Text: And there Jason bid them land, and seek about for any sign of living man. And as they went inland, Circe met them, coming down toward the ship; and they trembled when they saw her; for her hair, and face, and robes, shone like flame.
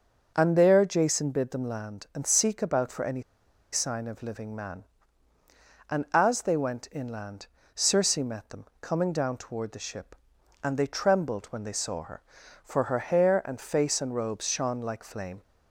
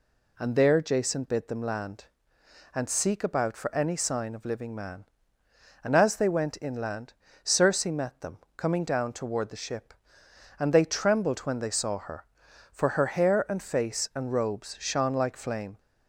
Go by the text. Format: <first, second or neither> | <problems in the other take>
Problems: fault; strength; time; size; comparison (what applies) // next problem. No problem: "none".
second | starts louder than the rest; until 1.3 s; 6.5 dB // pauses between "any" and "sign"; noticeable; at 3.2 s; 0.51 s long